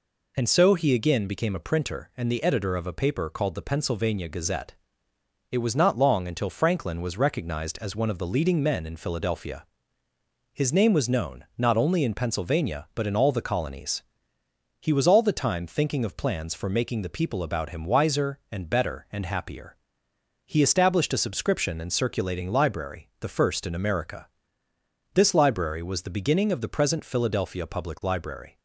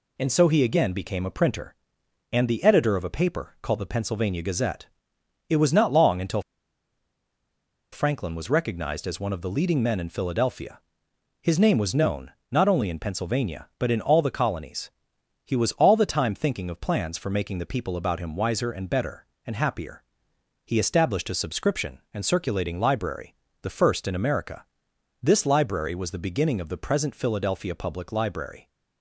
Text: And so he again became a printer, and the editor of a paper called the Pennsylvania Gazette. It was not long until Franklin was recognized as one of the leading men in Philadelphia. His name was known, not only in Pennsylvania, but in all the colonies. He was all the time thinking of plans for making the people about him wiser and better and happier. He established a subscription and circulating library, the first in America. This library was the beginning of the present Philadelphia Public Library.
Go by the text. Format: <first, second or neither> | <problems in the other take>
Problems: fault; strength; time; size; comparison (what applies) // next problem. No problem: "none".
first | pauses between "until" and "Franklin"; strong; at 6.4 s; 1.4 s long